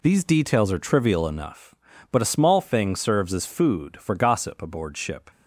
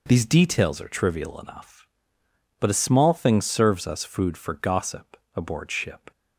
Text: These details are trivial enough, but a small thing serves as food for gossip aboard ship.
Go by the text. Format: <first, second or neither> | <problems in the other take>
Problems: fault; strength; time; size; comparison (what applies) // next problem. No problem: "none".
first | says "us" for "as"; at 3.8 s // pauses between "gossip" and "aboard"; slight; at 5.1 s; 0.18 s long